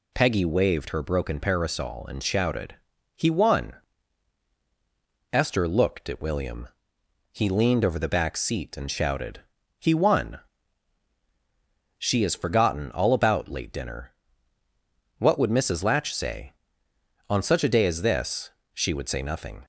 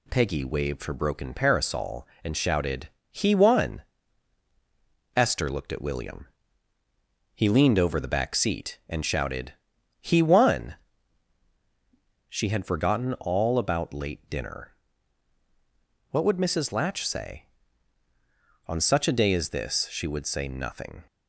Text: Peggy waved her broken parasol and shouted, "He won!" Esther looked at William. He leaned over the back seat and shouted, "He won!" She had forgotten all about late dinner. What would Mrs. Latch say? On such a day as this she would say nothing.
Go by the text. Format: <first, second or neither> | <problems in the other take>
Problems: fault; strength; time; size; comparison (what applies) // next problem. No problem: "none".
second | says "has" for "had"; at 12.2 s // pauses between "this" and "she"; slight; at 18.5 s; 0.22 s long